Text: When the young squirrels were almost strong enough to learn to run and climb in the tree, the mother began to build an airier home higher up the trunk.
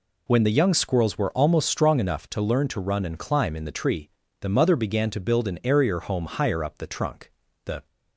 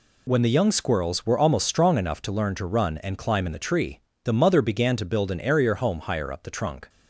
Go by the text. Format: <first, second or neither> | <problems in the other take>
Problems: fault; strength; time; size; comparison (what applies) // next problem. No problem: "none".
second | goes on to say "The"; slight; from 7.6 s on; 0.22 s long